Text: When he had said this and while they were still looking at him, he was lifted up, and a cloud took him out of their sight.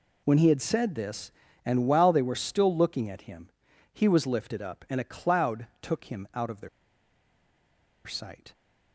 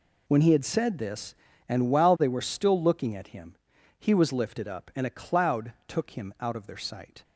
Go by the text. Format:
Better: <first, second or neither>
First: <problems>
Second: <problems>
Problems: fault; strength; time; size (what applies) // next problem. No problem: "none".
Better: second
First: pauses between "their" and "sight"; strong; at 6.6 s; 1.3 s long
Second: none